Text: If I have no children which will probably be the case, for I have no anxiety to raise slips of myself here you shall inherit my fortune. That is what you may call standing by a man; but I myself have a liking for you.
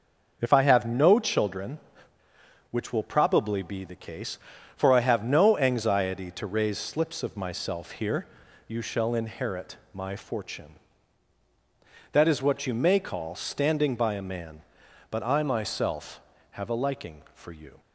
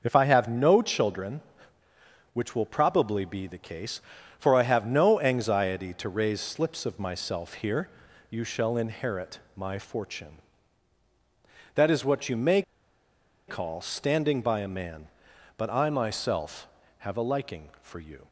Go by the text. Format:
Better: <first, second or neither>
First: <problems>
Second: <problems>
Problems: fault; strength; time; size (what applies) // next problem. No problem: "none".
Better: first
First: pauses between "here" and "you"; at 8.2 s; 0.42 s long // pauses between "inherit" and "my"; slight; at 9.7 s; 0.16 s long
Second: pauses between "here" and "you"; at 7.8 s; 0.42 s long // pauses between "inherit" and "my"; slight; at 9.3 s; 0.16 s long // pauses between "may" and "call"; noticeable; at 12.6 s; 0.86 s long